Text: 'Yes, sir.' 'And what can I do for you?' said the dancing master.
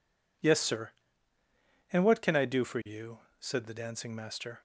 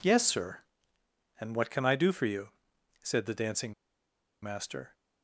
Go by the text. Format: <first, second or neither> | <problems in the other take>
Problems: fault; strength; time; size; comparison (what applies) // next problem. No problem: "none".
first | pauses between "dancing" and "master"; noticeable; at 3.7 s; 0.69 s long